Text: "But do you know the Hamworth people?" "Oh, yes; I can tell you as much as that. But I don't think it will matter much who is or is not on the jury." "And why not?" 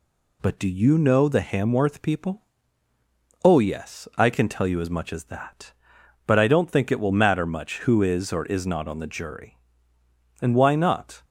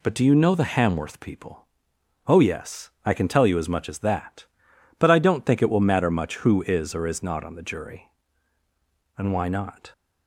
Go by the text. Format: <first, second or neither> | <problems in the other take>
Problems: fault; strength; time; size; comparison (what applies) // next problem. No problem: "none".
neither | none